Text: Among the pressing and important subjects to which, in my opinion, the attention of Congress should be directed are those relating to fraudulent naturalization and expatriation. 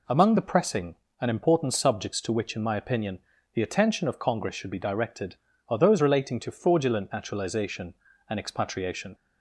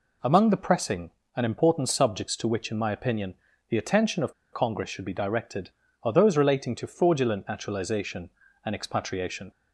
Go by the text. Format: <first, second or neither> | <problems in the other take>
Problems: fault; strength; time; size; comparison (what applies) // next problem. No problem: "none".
first | pauses between "of" and "Congress"; slight; at 4.3 s; 0.19 s long